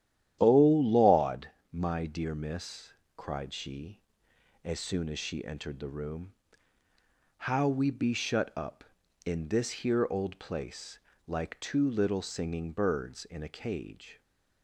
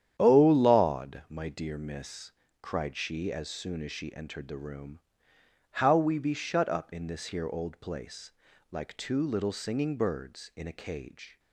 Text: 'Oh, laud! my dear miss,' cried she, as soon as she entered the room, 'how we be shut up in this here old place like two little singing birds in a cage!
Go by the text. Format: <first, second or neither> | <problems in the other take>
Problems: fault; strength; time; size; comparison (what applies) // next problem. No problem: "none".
neither | starts louder than the rest; strong; the same in both // pauses between "place" and "like"; the same in both